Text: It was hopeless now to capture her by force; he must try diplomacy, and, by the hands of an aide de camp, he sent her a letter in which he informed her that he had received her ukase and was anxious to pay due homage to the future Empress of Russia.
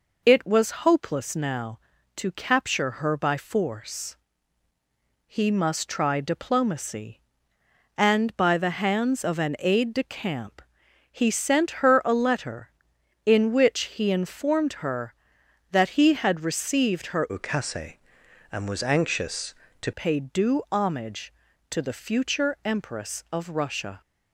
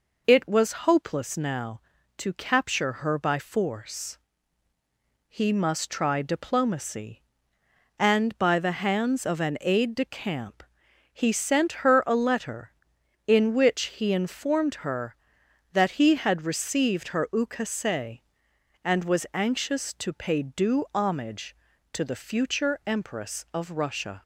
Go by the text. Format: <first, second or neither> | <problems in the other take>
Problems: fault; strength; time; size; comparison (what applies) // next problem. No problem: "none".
second | changes voice from "ukase" to "to"; from 17.2 to 19.9 s; 2.7 s long